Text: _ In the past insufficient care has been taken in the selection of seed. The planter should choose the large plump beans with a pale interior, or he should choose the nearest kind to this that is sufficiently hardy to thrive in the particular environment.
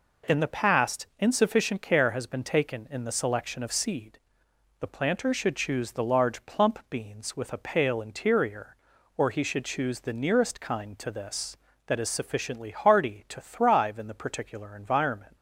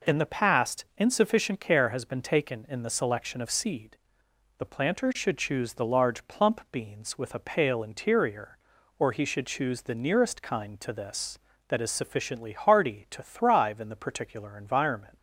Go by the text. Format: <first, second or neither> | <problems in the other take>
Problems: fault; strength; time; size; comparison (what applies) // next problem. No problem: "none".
neither | none